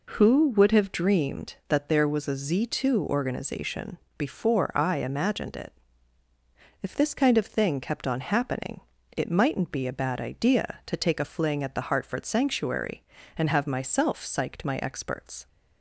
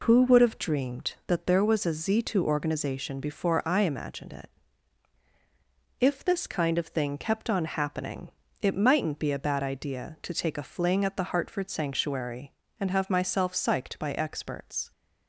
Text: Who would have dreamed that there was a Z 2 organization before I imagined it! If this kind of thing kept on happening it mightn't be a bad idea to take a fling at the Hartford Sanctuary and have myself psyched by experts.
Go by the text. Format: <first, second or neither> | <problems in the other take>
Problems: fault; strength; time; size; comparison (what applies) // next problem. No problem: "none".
second | pauses between "organization" and "before"; slight; at 3.9 s; 0.18 s long // pauses between "happening" and "it"; slight; at 8.8 s; 0.34 s long; slight in the second // says "my" for "by"; at 14.6 s